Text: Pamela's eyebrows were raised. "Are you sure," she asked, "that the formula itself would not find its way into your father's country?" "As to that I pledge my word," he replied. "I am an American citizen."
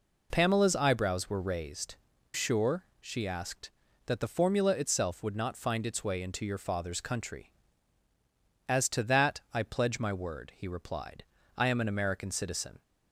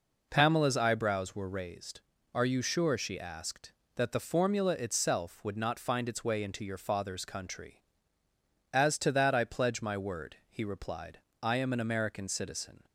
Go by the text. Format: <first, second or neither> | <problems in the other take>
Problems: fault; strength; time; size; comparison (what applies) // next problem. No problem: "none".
second | skips "Are you"; at 2.1 s